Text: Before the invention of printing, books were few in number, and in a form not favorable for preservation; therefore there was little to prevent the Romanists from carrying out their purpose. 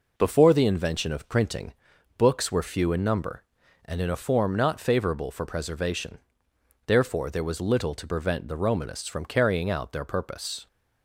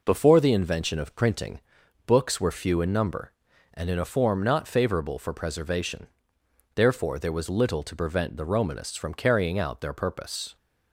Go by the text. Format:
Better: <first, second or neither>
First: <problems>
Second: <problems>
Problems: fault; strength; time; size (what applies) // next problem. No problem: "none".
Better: neither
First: none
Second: none